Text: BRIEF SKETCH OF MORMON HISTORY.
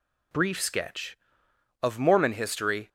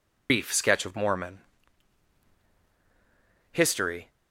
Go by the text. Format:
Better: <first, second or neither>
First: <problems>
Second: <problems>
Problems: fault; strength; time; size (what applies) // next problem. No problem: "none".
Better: first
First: none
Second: loses the start of "BRIEF"; at 0.2 s; 115 ms // pauses between "MORMON" and "HISTORY"; strong; at 1.4 s; 2.1 s long